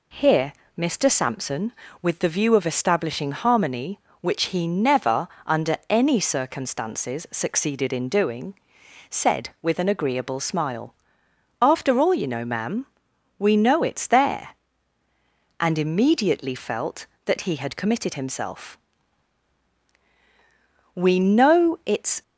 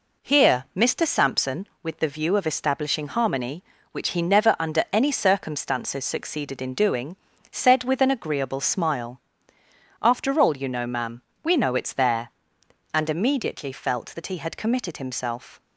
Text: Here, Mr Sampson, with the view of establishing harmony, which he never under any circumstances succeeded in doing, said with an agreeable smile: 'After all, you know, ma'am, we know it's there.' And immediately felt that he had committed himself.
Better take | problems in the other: second | pauses between "never" and "under"; slight; at 5.2 s; 0.20 s long // goes on to say "We know it's"; noticeable; from 20.9 s on; 1.2 s long

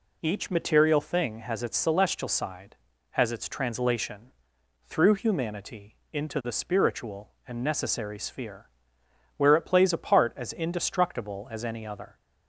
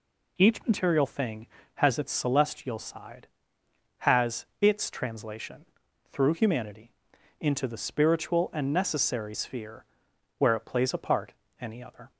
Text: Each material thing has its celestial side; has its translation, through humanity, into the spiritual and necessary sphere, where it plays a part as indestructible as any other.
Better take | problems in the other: first | skips "as indestructible as"; at 11.4 s

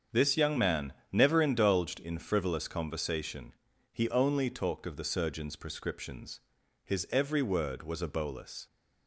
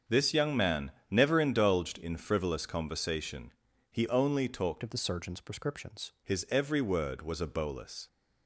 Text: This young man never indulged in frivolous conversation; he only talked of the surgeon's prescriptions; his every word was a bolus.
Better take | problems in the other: first | starts louder than the rest; until 1.2 s; 7 dB; strong in the first // pauses between "man" and "never"; slight; at 0.9 s; 0.20 s long; slight in the first // changes voice from "of" to "prescriptions"; from 4.8 to 6.1 s; 1.3 s long

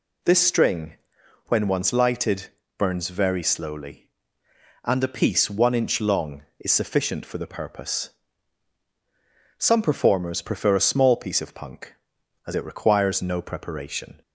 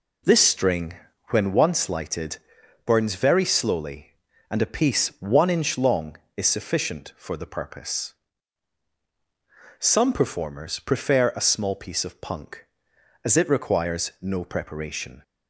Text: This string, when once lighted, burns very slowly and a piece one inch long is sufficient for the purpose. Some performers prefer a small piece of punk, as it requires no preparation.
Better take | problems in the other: first | starts louder than the rest; noticeable; until 1.8 s; 4 dB

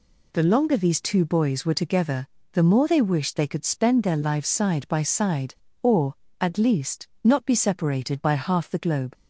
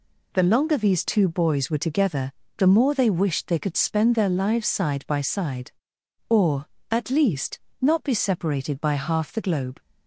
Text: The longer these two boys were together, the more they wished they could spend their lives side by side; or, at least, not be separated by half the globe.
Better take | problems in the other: neither | none

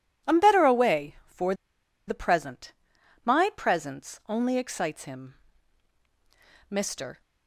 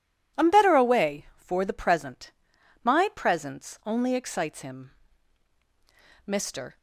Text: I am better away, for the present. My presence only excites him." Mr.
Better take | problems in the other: second | pauses between "for" and "the"; noticeable; at 1.5 s; 0.54 s long

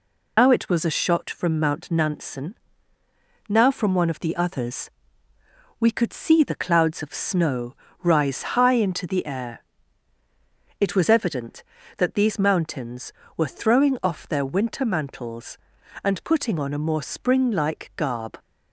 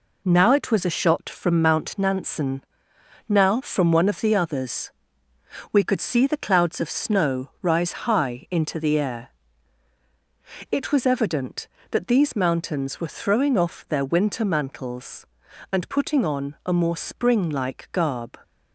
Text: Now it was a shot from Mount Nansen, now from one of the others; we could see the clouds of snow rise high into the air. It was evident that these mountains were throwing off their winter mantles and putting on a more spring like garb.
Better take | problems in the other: second | loses the start of "Now"; at 0.3 s; 140 ms // pauses between "snow" and "rise"; slight; at 7.7 s; 0.30 s long

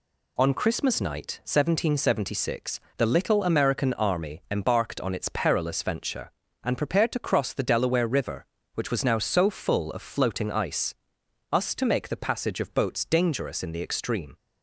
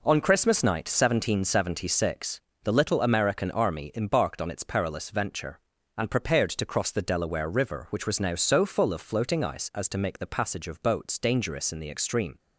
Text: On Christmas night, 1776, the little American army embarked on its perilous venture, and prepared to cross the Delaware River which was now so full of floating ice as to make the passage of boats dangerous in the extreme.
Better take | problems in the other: second | says "us" for "as"; at 11.5 s

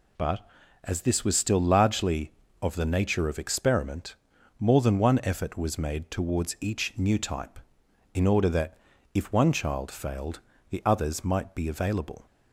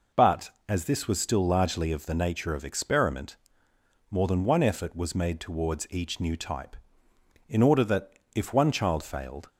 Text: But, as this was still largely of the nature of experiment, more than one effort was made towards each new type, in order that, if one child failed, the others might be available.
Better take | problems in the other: first | stops before "the others might be available"; at 9.4 s

